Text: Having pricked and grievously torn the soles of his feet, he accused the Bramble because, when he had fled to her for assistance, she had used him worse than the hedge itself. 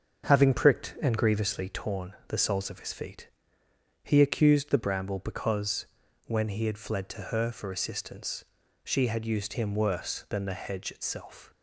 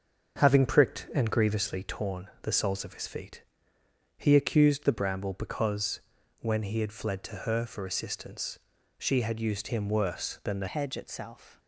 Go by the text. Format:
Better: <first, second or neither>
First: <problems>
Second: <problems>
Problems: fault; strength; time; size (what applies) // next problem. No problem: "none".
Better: first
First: starts louder than the rest; until 1.3 s; 7 dB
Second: starts louder than the rest; until 1.4 s; 6.5 dB // changes voice at "hedge"; from 10.6 s on; 0.9 s long